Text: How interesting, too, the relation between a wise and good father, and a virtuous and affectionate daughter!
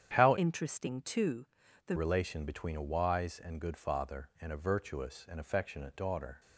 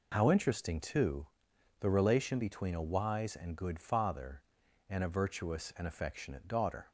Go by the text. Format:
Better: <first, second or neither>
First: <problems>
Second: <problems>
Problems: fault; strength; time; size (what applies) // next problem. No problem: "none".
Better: second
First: starts louder than the rest; strong; until 1.1 s; 9 dB // changes voice from "interesting" to "the"; from 0.3 to 1.9 s; 1.6 s long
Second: none